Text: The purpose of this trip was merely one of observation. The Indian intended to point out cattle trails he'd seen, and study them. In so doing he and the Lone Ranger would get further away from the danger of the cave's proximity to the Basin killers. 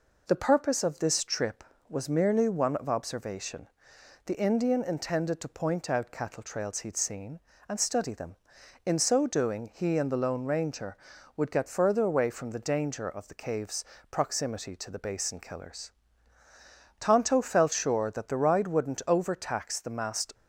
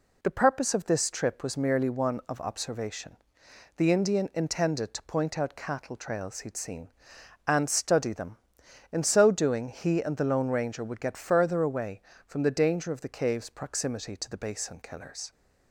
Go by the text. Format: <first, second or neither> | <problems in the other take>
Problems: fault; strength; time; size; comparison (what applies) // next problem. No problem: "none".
second | pauses between "cave's" and "proximity"; slight; at 13.8 s; 0.26 s long // goes on to say "Tonto felt sure that the ride wouldn't overtax the masked"; strong; from 16.9 s on; 3.3 s long